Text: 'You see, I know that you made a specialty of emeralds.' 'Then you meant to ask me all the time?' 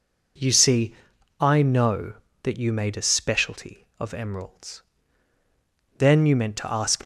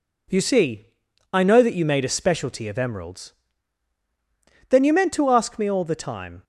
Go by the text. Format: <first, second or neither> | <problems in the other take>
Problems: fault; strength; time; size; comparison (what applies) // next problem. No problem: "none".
second | stops before "me all the time"; at 7.0 s